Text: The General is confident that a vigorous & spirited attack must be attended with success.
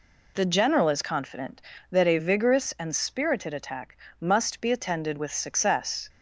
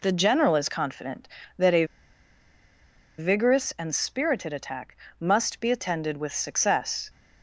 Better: first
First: pauses between "attack" and "must"; slight; at 3.9 s; 0.20 s long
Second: pauses between "a" and "vigorous"; strong; at 1.8 s; 1.3 s long // pauses between "attack" and "must"; slight; at 4.9 s; 0.20 s long

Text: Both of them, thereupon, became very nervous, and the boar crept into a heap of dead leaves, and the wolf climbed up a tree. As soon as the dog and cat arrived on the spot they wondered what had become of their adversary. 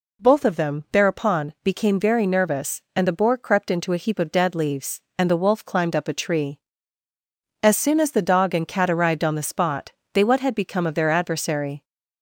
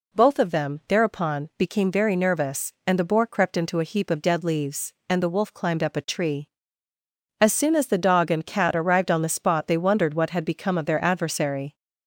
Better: second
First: pauses between "spot" and "they"; slight; at 9.9 s; 0.22 s long // skips "wondered"; at 10.2 s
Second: none

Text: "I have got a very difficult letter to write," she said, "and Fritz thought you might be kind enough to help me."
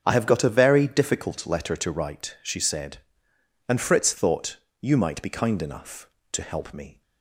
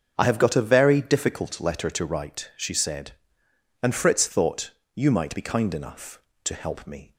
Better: neither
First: starts louder than the rest; until 1.0 s; 7 dB // pauses between "thought" and "you"; slight; at 4.5 s; 0.24 s long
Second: starts louder than the rest; until 1.1 s; 7 dB // pauses between "thought" and "you"; slight; at 4.6 s; 0.24 s long

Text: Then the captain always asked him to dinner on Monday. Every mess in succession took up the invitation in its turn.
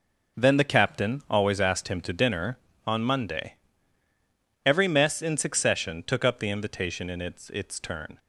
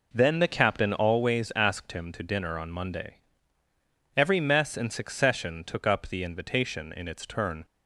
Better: second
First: says "its" twice; at 7.5 s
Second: none

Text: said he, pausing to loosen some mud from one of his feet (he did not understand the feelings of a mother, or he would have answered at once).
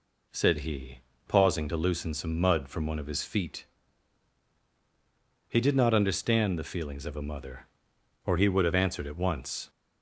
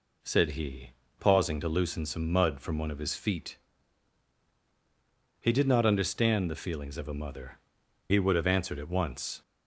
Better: first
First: none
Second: skips "or"; at 7.8 s

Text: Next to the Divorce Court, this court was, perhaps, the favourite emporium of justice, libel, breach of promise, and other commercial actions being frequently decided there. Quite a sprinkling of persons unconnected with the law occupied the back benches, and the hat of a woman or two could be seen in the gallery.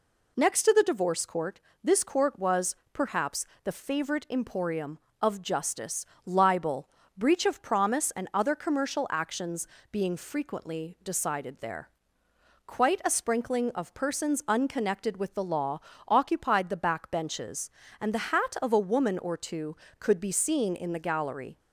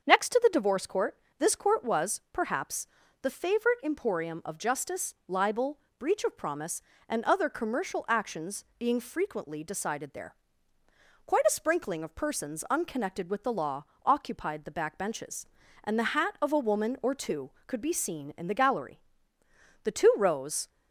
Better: first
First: pauses between "actions" and "being"; slight; at 9.6 s; 0.24 s long // pauses between "law" and "occupied"; slight; at 15.7 s; 0.30 s long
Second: starts louder than the rest; until 1.0 s; 7 dB // pauses between "actions" and "being"; slight; at 8.6 s; 0.16 s long // pauses between "law" and "occupied"; slight; at 13.8 s; 0.20 s long // goes on to say "The two rows"; noticeable; from 19.8 s on; 0.84 s long

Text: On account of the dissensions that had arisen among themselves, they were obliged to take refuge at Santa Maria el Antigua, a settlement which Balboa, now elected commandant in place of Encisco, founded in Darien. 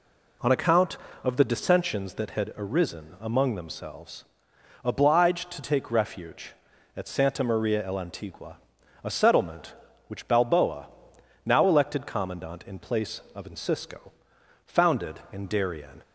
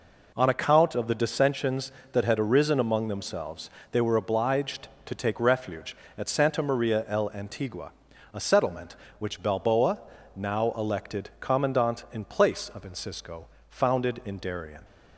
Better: second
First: skips "they were"; at 4.5 s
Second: none

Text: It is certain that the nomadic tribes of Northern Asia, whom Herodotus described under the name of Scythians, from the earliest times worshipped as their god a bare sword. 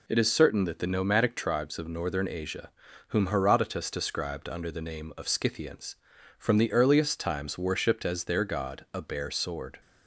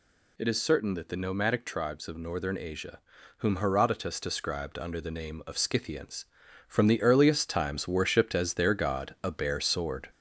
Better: first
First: none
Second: gets louder; slight; throughout; 3 dB

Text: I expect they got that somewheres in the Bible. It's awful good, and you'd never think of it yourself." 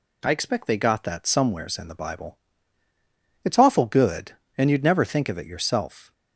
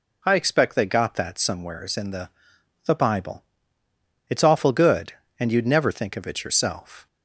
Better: first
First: none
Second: says "the" twice; at 2.8 s

